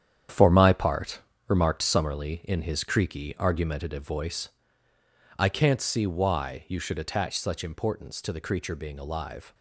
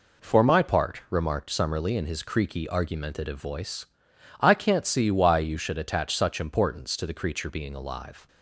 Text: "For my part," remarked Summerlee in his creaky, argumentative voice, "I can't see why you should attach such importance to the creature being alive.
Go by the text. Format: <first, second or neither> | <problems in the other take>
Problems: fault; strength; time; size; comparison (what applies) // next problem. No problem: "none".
second | gets quieter; strong; throughout; 9 dB